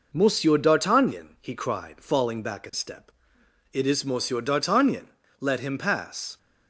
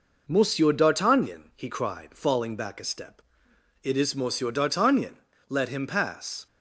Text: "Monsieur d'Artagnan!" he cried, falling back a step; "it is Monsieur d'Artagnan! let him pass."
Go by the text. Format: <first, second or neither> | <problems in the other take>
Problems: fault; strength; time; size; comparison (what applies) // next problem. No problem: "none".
neither | none